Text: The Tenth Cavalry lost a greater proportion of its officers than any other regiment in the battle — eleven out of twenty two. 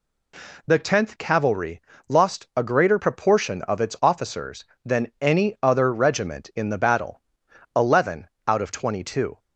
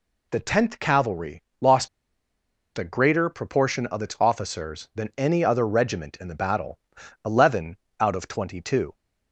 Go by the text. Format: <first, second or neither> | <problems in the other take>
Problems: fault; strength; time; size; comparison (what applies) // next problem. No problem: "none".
first | pauses between "Cavalry" and "lost"; slight; at 1.4 s; 0.18 s long; slight in the first // pauses between "lost" and "a"; noticeable; at 1.8 s; 0.89 s long // pauses between "eleven" and "out"; slight; at 7.7 s; 0.24 s long; slight in the first